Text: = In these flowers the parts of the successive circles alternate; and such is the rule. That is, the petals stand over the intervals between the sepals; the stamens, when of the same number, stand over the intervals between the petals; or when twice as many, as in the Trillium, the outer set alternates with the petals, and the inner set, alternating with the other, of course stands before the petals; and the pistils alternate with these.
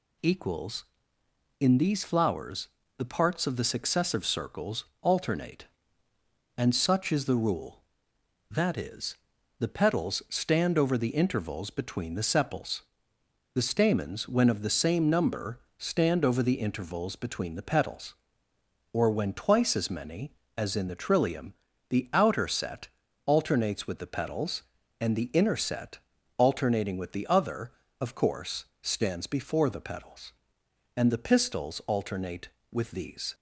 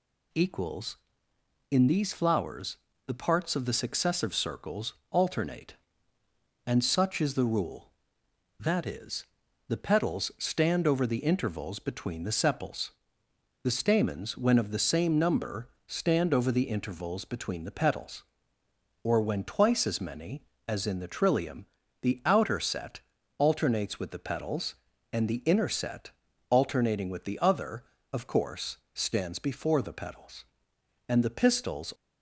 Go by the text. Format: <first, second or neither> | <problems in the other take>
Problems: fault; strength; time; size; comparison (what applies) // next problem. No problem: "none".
first | pauses between "flowers" and "the"; slight; at 2.7 s; 0.30 s long; slight in the first // pauses between "circles" and "alternate"; slight; at 4.9 s; 0.16 s long; slight in the first // pauses between "set" and "alternates"; at 22.9 s; 0.38 s long; also in the first // pauses between "course" and "stands"; slight; at 28.7 s; 0.18 s long; slight in the first // stops before "alternate with these"; at 31.9 s